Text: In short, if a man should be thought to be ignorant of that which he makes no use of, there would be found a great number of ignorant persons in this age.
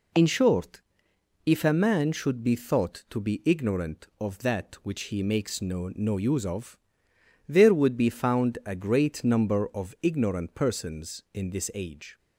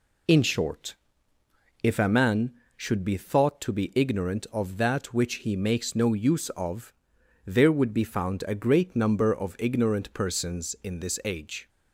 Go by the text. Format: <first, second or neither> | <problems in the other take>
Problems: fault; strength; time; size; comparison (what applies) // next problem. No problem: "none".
second | says "no" twice; at 5.9 s